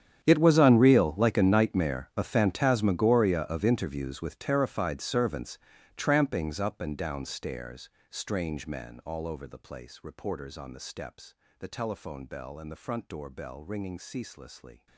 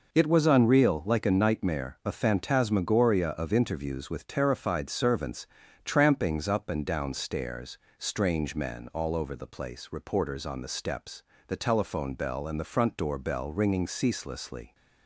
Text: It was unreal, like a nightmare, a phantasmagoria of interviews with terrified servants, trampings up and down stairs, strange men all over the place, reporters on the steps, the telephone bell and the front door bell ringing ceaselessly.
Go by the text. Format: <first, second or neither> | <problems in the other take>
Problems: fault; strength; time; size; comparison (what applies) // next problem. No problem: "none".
second | gets quieter; strong; throughout; 20 dB